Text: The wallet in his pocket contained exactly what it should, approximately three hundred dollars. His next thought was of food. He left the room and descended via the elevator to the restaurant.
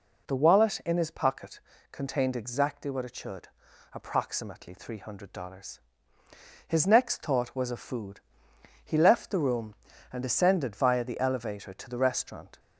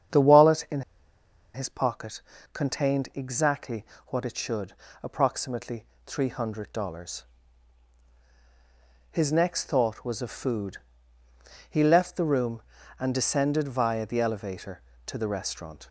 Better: first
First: pauses between "pocket" and "contained"; slight; at 1.5 s; 0.32 s long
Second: starts louder than the rest; strong; until 1.8 s; 8.5 dB // pauses between "in" and "his"; noticeable; at 0.8 s; 0.73 s long // pauses between "pocket" and "contained"; slight; at 2.2 s; 0.32 s long // pauses between "exactly" and "what"; slight; at 3.8 s; 0.24 s long // pauses between "approximately" and "three"; slight; at 5.8 s; 0.24 s long

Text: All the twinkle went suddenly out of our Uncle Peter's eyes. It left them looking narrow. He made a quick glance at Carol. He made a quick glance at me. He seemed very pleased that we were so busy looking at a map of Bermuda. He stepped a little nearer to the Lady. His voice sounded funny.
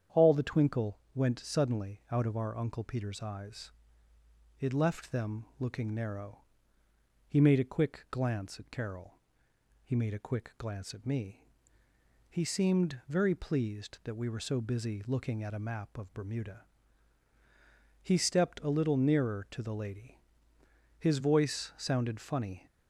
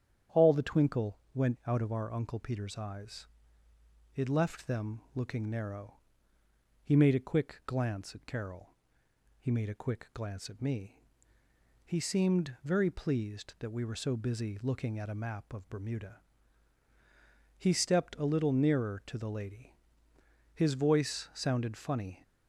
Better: first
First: starts louder than the rest; strong; until 1.2 s; 8.5 dB // pauses between "twinkle" and "went"; slight; at 0.9 s; 0.16 s long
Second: starts louder than the rest; strong; until 1.4 s; 9 dB // pauses between "twinkle" and "went"; slight; at 1.1 s; 0.16 s long // skips "suddenly"; at 1.6 s

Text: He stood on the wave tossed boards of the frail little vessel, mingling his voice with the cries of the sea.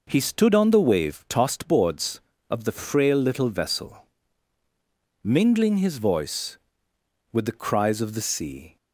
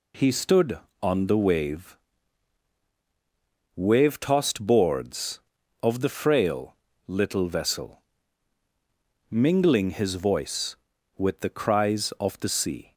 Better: first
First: none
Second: says "wave" twice; at 3.7 s // pauses between "frail" and "little"; slight; at 6.7 s; 0.32 s long

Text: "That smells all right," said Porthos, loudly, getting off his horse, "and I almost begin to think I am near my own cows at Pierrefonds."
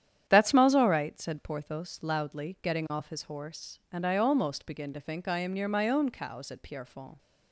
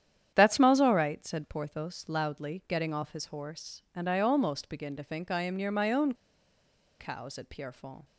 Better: first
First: starts louder than the rest; strong; until 1.2 s; 9.5 dB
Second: starts louder than the rest; strong; until 1.3 s; 9.5 dB // pauses between "own" and "cows"; noticeable; at 6.1 s; 0.86 s long

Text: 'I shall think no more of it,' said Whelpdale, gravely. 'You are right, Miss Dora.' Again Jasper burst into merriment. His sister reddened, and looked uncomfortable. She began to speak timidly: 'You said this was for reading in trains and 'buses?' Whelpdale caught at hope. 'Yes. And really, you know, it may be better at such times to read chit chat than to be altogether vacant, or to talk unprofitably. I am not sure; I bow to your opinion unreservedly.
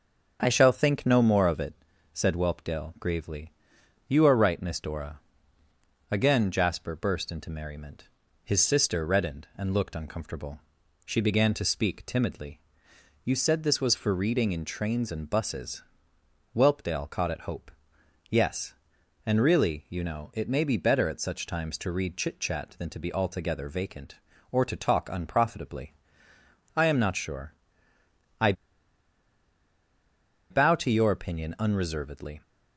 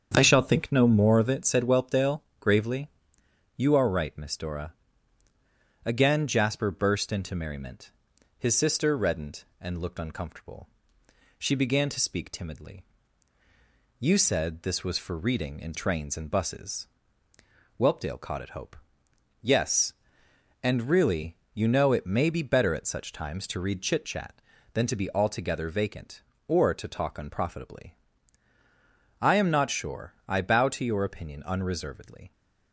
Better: second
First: starts louder than the rest; until 1.4 s; 6.5 dB // pauses between "I" and "bow"; strong; at 28.5 s; 1.9 s long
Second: starts louder than the rest; strong; until 1.1 s; 7.5 dB

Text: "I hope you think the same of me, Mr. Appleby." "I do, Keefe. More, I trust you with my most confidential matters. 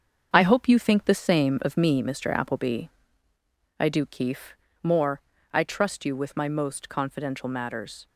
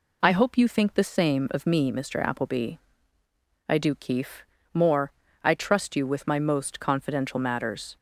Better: second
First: gets quieter; strong; throughout; 7.5 dB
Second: none

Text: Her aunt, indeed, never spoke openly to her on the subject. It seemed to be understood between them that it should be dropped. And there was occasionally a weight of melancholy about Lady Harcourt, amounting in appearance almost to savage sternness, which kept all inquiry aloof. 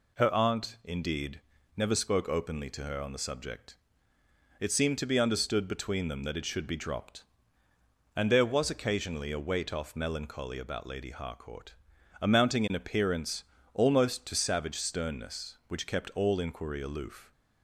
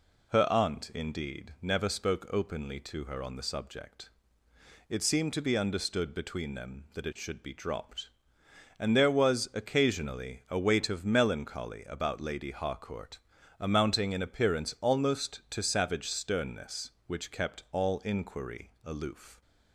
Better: second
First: says "off" for "of"; at 9.7 s // pauses between "appearance" and "almost"; slight; at 13.4 s; 0.30 s long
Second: none

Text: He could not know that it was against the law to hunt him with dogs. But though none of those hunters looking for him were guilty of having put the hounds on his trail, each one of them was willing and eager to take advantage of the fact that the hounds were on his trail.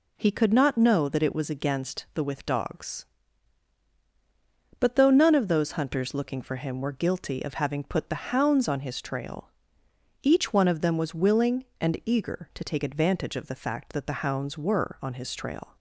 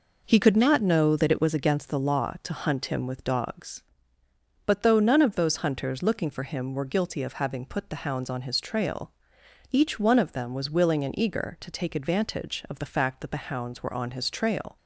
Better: second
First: skips "law to hunt him"; at 2.2 s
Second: none

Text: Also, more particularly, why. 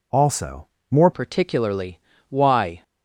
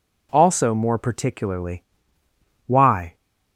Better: second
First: changes voice at "particularly"; from 1.1 s on; 1.7 s long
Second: none

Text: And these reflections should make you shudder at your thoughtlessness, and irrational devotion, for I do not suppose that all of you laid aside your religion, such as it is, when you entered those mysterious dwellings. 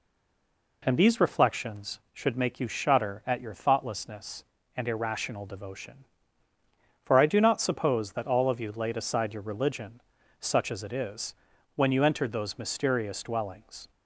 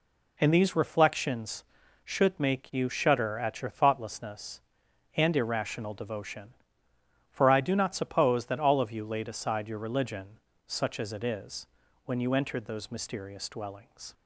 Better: second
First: stays silent before the first word; slight; until 0.8 s; 0.8 s long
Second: none

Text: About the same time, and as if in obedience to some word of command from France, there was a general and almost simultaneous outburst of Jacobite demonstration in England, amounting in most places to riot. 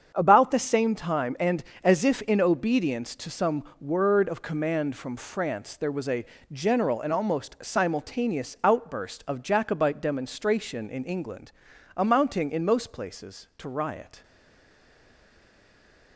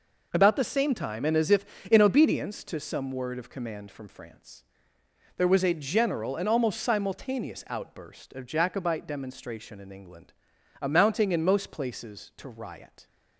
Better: second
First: starts louder than the rest; strong; until 1.1 s; 7 dB // pauses between "some" and "word"; slight; at 3.6 s; 0.18 s long // pauses between "a" and "general"; slight; at 6.2 s; 0.24 s long // stays silent after the last word; noticeable; from 14.2 s on; 1.9 s long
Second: none

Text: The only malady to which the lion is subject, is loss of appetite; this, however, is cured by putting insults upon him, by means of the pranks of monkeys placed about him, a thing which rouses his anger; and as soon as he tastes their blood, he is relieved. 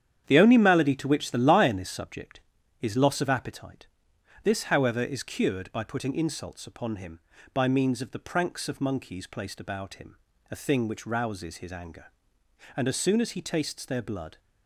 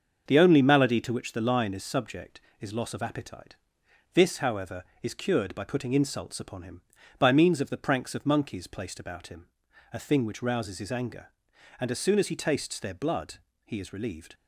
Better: second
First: starts louder than the rest; strong; until 1.2 s; 9 dB // stops before "he is relieved"; at 14.3 s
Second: starts louder than the rest; until 1.3 s; 6.5 dB

